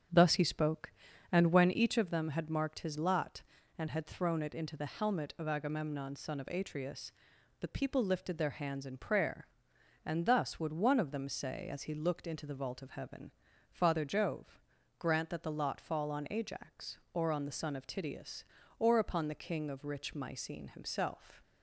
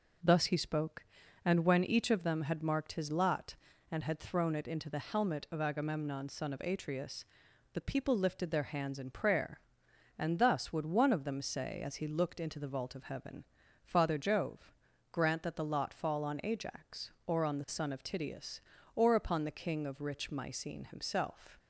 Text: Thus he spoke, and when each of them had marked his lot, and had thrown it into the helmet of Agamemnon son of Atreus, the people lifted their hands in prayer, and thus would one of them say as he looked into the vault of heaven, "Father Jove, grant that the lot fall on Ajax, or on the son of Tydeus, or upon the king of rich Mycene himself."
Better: second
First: starts louder than the rest; strong; until 2.0 s; 7.5 dB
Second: none

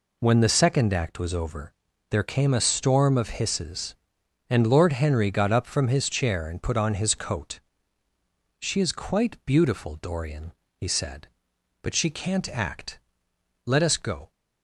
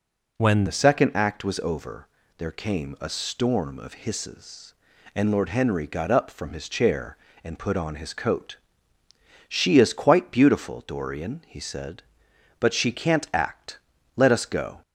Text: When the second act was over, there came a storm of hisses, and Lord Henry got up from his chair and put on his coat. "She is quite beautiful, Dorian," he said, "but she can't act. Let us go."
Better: first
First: none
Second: changes voice at "the"; from 0.6 s on; 14.2 s long

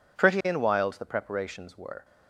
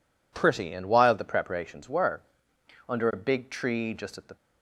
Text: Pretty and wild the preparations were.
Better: first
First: none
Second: goes on to say "Under a big tree just at the"; from 2.8 s on; 1.4 s long

